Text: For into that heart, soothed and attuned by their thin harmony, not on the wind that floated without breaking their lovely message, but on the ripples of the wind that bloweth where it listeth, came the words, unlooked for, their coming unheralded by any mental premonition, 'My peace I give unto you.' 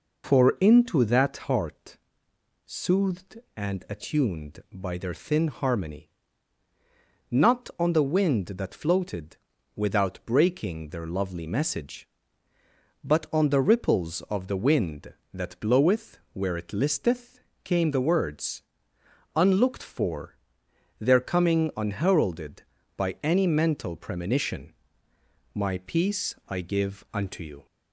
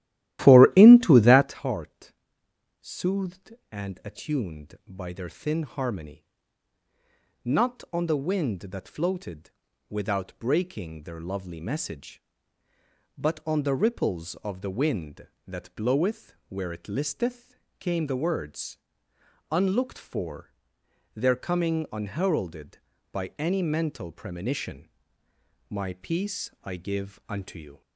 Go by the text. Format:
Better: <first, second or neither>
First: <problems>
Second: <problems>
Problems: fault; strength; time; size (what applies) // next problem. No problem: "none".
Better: first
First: pauses between "floated" and "without"; at 9.3 s; 0.38 s long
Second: starts louder than the rest; strong; until 1.6 s; 14 dB // pauses between "floated" and "without"; at 9.5 s; 0.38 s long